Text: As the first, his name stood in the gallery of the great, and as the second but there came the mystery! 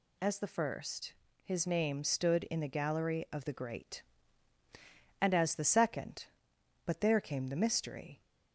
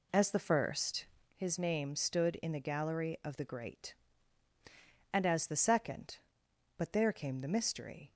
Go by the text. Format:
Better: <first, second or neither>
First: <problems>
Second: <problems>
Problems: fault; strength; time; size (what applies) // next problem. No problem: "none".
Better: first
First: none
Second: starts louder than the rest; slight; until 1.5 s; 2.5 dB